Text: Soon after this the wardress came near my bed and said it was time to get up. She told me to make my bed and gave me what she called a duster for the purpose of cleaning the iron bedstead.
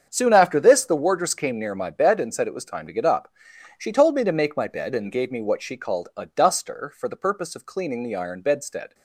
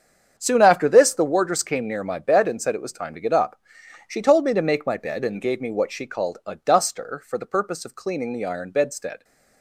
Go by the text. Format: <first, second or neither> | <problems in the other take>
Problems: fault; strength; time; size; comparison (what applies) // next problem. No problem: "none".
neither | starts louder than the rest; strong; the same in both